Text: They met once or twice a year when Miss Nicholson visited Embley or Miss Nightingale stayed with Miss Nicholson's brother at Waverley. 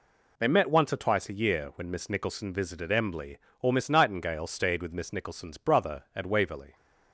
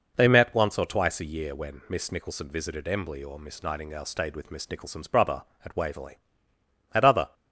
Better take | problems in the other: first | goes on to say "At other"; slight; from 6.9 s on; 0.40 s long

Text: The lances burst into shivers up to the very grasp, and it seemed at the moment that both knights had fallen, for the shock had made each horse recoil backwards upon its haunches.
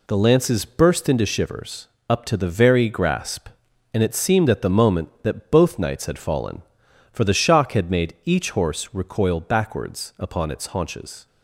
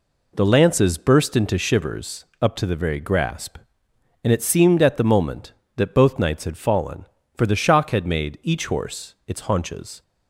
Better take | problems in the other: first | pauses between "shivers" and "up"; slight; at 2.2 s; 0.18 s long; slight in the first // skips "recoil backwards upon"; at 9.2 s

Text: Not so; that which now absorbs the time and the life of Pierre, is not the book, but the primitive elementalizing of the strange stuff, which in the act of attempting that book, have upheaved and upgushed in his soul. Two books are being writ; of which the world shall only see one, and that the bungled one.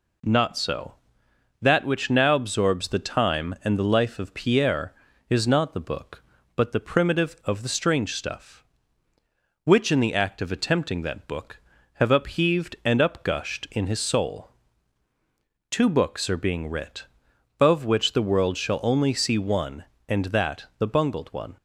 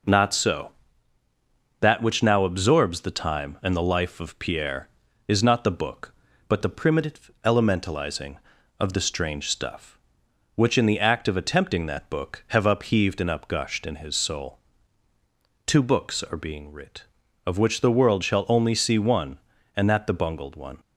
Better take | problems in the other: second | skips "elementalizing"; at 7.4 s

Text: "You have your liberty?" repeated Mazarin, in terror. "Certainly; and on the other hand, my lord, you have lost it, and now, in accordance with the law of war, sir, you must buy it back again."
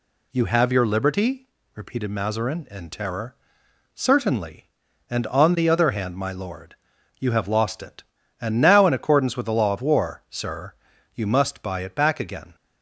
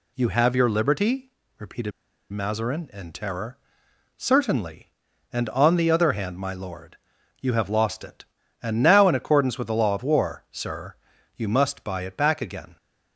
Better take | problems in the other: first | pauses between "repeated" and "Mazarin"; at 1.9 s; 0.41 s long

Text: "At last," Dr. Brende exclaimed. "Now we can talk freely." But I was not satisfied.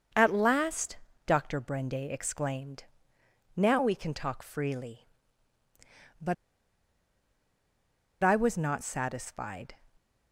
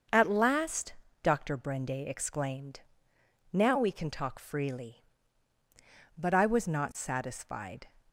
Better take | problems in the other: second | starts louder than the rest; until 1.4 s; 6.5 dB; also in the second // pauses between "But" and "I"; strong; at 6.3 s; 1.8 s long

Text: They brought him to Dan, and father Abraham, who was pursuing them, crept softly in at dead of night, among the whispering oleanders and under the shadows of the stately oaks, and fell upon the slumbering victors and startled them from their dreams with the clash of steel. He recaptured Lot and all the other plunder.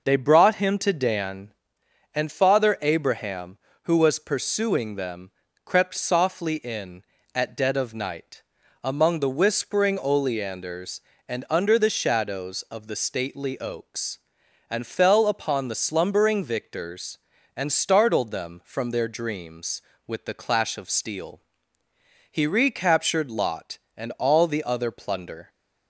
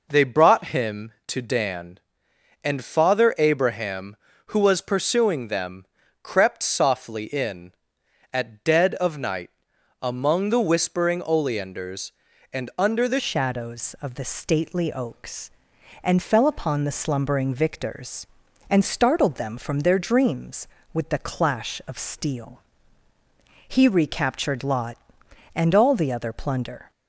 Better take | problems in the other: first | changes voice at "shadows"; from 13.1 s on; 13.8 s long

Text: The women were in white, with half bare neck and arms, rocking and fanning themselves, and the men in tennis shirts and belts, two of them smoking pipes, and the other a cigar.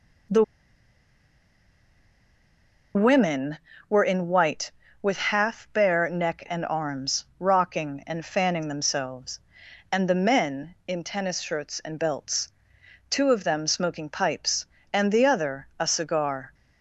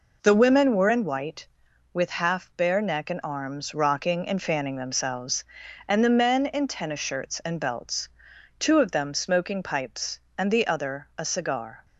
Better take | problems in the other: second | pauses between "The" and "women"; strong; at 0.4 s; 2.5 s long

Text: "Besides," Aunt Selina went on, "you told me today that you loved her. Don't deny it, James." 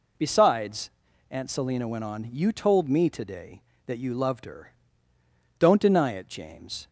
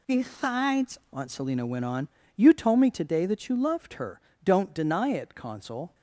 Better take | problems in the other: first | says "Consul" for "James"; at 5.3 s

